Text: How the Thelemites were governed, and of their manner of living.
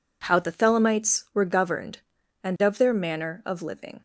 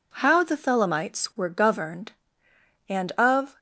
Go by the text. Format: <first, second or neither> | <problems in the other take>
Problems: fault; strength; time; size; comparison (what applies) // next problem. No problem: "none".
first | stops before "their manner of living"; at 3.5 s